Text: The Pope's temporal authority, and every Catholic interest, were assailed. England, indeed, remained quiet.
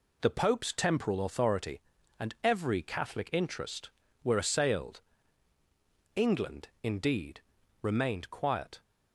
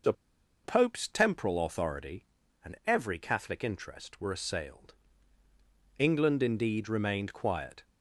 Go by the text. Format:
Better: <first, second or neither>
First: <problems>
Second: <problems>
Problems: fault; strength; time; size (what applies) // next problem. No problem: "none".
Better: first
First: none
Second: pauses between "The" and "Pope's"; noticeable; at 0.1 s; 0.51 s long